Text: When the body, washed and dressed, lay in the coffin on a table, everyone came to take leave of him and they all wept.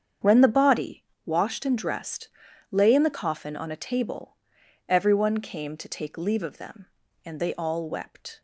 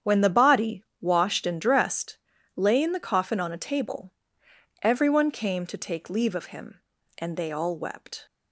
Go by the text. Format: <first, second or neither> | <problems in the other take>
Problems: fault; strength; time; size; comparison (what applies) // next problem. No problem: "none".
second | starts louder than the rest; strong; until 1.4 s; 8 dB; strong in the second // says "them" for "him"; at 6.5 s